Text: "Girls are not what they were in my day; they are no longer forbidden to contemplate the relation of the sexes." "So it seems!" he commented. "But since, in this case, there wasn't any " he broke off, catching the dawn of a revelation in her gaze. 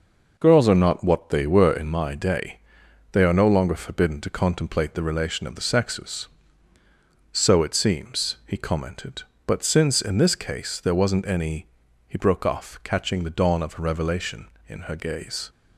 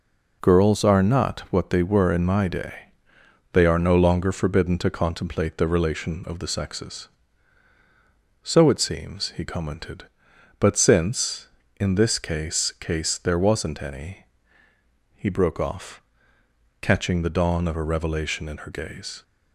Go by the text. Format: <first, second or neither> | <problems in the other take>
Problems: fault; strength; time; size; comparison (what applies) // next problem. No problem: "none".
first | says "case" twice; at 12.7 s